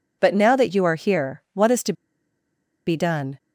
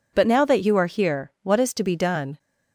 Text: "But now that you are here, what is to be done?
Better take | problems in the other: second | pauses between "to" and "be"; noticeable; at 1.9 s; 0.93 s long

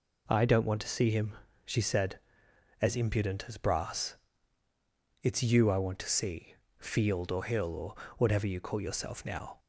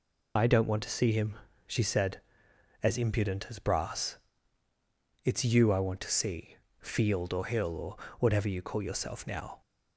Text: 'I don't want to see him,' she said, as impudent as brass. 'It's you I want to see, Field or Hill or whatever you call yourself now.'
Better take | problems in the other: first | loses the start of "I"; at 0.3 s; 80 ms // pauses between "or" and "whatever"; slight; at 7.9 s; 0.22 s long; slight in the first

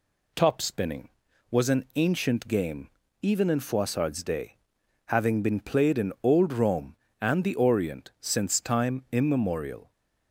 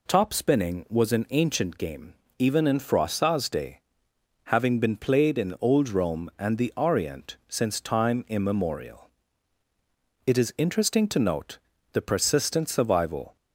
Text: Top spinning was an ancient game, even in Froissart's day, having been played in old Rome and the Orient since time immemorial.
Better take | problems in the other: first | goes on to say "It is interesting to note the persistent survival"; strong; from 10.2 s on; 3.1 s long

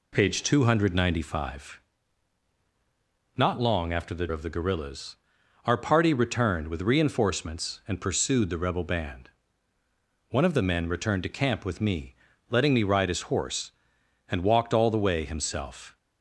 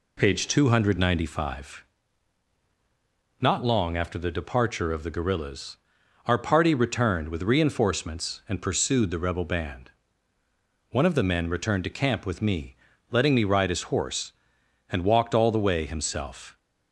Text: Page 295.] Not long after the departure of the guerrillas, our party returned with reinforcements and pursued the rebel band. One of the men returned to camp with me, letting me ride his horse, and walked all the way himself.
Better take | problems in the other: second | skips "departure"; at 4.2 s

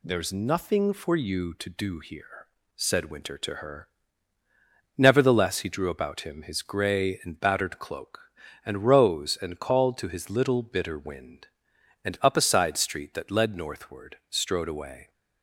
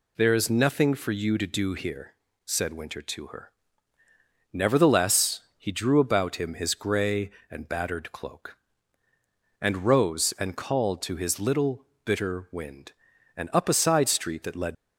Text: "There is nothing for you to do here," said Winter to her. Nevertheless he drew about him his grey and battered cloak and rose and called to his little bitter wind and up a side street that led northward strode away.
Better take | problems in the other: first | pauses between "Nevertheless" and "he"; slight; at 5.4 s; 0.16 s long // pauses between "little" and "bitter"; slight; at 11.8 s; 0.20 s long // stops before "northward strode away"; at 14.7 s

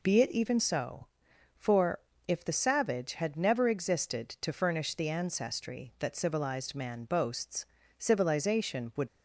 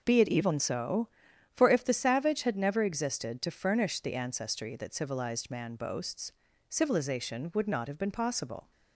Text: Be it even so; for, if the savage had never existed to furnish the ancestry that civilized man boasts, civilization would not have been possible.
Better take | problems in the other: second | stops before "not have been possible"; at 9.0 s

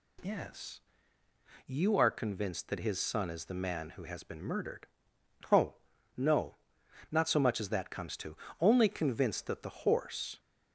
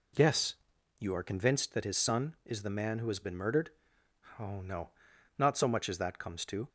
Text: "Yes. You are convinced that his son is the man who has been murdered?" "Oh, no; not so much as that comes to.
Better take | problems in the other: second | goes on to say "Only convinced that the horse"; strong; from 8.5 s on; 1.8 s long

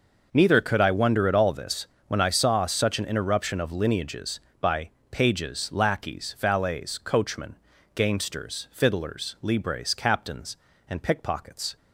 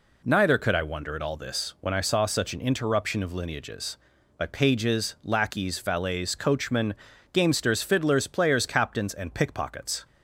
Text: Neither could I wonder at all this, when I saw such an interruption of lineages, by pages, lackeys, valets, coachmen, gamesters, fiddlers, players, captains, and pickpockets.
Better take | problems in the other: second | pauses between "by" and "pages"; slight; at 4.8 s; 0.20 s long // says "libres" for "players"; at 9.4 s

